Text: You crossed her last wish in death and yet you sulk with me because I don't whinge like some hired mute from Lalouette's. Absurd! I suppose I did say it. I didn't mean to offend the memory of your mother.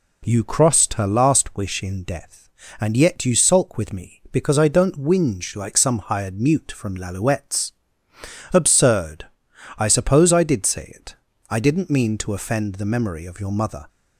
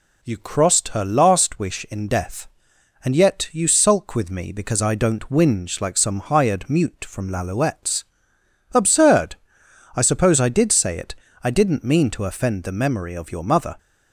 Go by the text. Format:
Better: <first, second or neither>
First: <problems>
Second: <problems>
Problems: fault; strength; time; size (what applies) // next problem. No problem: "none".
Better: neither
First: none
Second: none